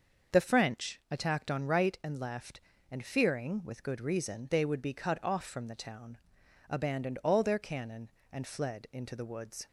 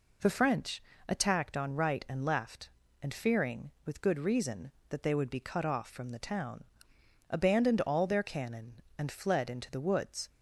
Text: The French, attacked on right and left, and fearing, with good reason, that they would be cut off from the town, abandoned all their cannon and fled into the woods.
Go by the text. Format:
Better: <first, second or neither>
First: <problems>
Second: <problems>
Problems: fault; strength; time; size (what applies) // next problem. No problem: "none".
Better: second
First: starts louder than the rest; until 1.4 s; 6.5 dB // skips "that"; at 4.5 s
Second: none